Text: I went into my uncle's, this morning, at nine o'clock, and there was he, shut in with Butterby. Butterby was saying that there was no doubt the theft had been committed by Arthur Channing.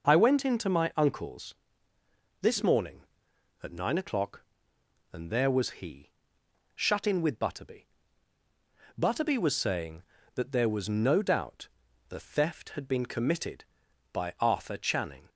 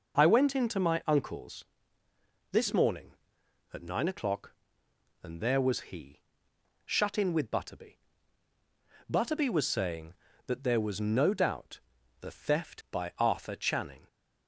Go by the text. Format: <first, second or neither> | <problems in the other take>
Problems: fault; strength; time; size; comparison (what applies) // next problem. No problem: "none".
first | pauses between "doubt" and "the"; at 11.7 s; 0.42 s long; also in the first // skips "had been committed"; at 12.8 s